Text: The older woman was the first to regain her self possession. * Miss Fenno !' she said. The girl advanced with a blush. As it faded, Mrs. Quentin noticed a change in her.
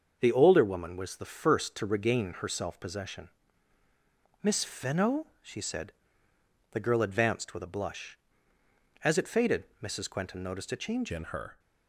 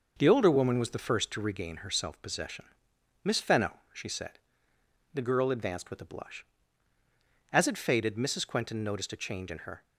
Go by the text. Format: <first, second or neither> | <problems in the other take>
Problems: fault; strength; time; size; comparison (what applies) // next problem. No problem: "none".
second | starts louder than the rest; until 1.2 s; 6.5 dB // changes voice at "in"; from 11.1 s on; 0.4 s long